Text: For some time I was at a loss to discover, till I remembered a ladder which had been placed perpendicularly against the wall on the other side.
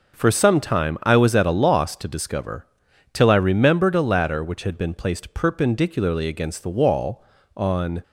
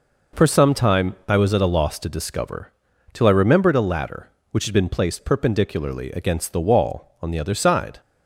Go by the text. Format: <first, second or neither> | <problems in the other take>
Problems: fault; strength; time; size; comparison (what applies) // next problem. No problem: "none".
second | stops before "the other side"; at 8.0 s